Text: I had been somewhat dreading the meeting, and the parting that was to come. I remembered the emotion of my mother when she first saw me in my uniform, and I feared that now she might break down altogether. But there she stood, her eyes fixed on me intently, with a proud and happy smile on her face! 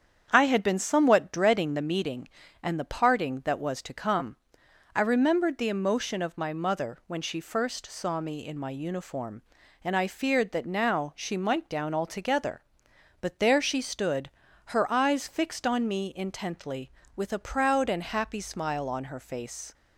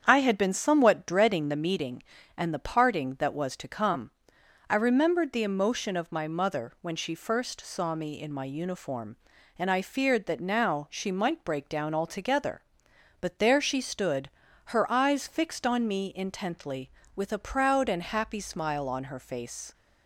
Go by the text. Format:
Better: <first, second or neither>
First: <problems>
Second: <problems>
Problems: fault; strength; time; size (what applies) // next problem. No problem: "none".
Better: second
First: starts louder than the rest; strong; until 1.3 s; 8 dB // skips "break"; at 11.7 s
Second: starts louder than the rest; strong; until 1.0 s; 8 dB